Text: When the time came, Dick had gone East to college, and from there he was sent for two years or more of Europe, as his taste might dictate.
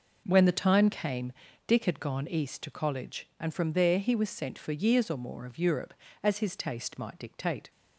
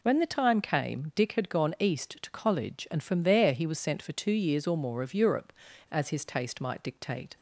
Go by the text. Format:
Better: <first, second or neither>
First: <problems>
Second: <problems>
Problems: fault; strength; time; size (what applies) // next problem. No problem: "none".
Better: second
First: skips "two"; at 4.7 s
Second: none